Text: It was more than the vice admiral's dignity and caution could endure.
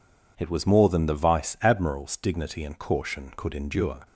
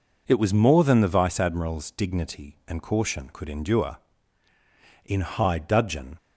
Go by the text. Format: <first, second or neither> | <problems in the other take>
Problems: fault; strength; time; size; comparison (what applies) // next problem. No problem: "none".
first | goes on to say "In high dudgeon"; noticeable; from 5.0 s on; 1.1 s long